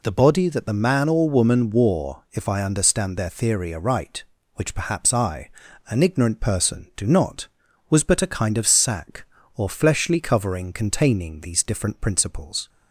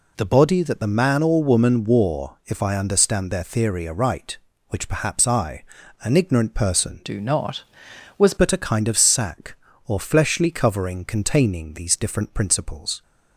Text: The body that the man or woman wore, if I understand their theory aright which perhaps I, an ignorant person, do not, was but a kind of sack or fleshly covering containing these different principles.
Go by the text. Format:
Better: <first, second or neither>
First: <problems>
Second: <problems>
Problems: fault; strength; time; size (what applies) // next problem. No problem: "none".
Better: first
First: none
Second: changes voice from "do" to "was"; from 7.0 to 8.3 s; 1.3 s long